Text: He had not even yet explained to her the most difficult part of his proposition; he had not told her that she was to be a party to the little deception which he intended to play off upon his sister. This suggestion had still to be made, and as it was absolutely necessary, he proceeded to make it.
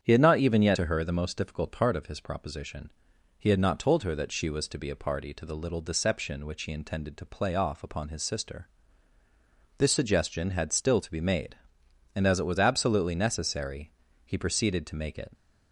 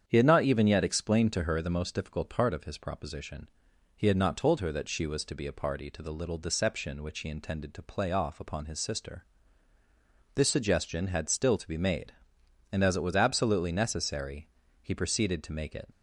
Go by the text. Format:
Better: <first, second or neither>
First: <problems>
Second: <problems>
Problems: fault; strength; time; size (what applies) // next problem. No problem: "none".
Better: second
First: starts louder than the rest; strong; until 1.0 s; 8.5 dB // skips "explained"; at 0.7 s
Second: starts louder than the rest; strong; until 1.0 s; 8.5 dB